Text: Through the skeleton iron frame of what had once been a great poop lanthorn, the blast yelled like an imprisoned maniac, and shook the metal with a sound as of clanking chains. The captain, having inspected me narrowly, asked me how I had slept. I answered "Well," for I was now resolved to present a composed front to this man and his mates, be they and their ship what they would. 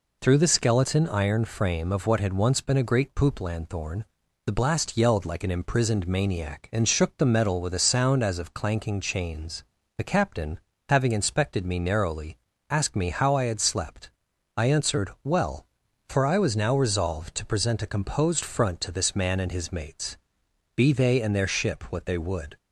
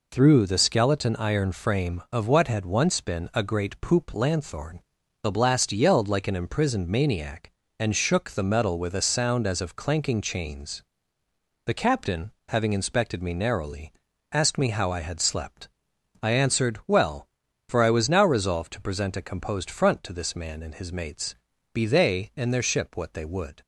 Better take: neither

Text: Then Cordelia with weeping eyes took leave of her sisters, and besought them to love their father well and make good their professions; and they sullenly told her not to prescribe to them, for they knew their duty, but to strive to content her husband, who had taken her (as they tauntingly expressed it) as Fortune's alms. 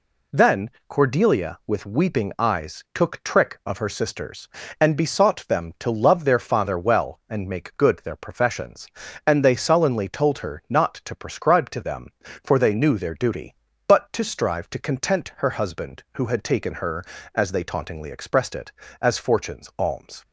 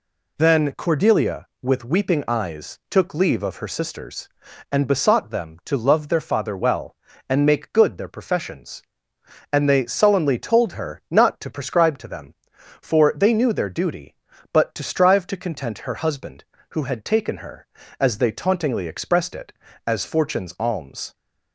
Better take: second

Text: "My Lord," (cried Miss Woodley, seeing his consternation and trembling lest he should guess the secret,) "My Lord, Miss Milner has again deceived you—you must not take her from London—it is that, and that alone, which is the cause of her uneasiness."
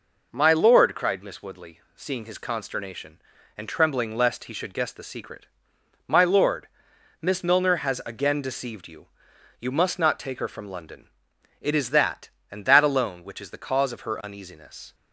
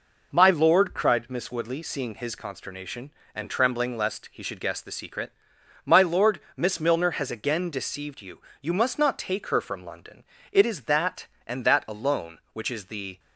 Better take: first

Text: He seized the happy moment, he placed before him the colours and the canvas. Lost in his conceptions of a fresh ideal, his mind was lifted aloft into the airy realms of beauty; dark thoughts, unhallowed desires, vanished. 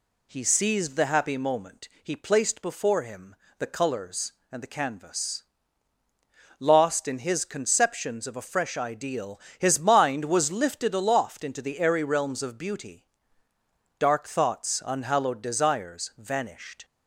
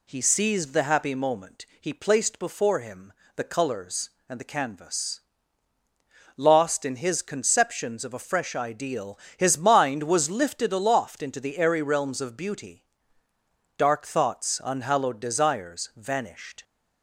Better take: neither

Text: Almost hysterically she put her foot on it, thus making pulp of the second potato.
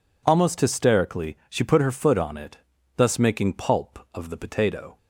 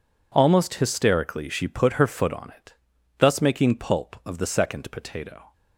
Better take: second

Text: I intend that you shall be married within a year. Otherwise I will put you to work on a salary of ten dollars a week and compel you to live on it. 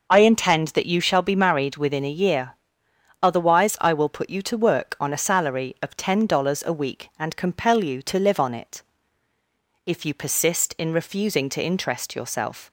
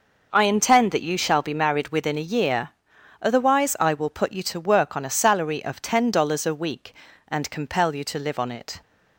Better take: second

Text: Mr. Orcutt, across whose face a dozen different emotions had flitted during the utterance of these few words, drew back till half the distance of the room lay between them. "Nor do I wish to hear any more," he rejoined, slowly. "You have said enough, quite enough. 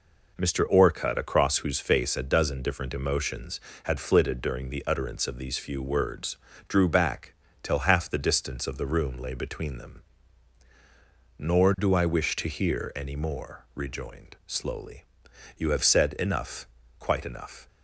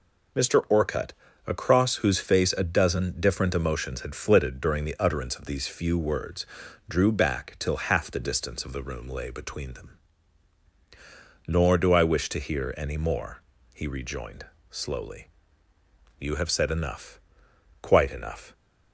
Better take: second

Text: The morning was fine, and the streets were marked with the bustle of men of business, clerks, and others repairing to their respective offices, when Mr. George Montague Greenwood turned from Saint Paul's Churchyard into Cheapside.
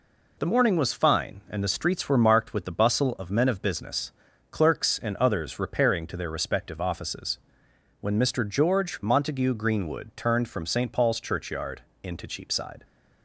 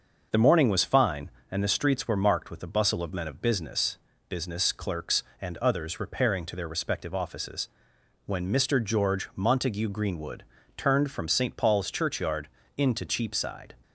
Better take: first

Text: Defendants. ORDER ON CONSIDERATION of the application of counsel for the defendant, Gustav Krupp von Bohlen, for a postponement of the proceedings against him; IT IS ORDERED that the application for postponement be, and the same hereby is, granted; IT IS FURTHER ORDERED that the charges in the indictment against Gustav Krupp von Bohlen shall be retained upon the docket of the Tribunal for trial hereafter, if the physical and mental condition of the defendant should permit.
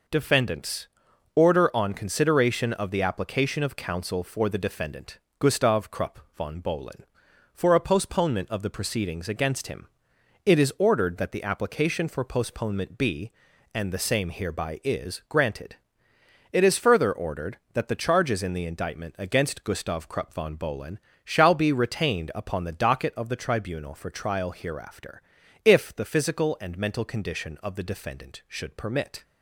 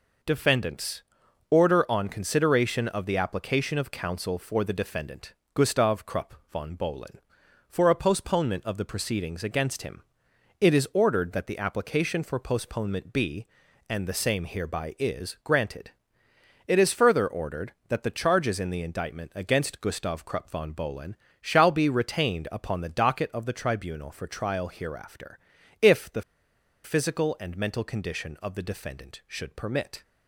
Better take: first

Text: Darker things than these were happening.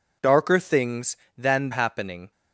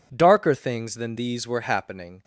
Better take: second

